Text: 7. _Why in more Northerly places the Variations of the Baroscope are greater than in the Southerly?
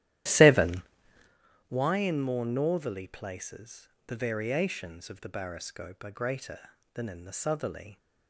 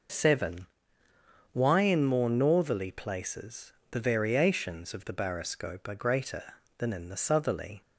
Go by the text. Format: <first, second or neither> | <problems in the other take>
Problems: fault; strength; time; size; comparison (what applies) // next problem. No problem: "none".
second | starts louder than the rest; strong; until 1.3 s; 13 dB // pauses between "places" and "the"; slight; at 3.8 s; 0.20 s long; slight in the second